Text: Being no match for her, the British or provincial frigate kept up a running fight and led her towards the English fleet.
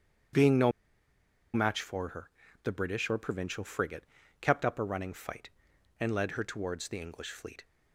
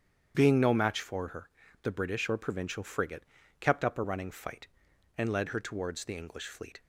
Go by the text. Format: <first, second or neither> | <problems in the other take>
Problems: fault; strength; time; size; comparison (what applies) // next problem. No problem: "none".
second | starts louder than the rest; strong; until 2.1 s; 8.5 dB; strong in the second // pauses between "no" and "match"; noticeable; at 0.7 s; 0.83 s long // pauses between "frigate" and "kept"; slight; at 4.0 s; 0.36 s long; slight in the second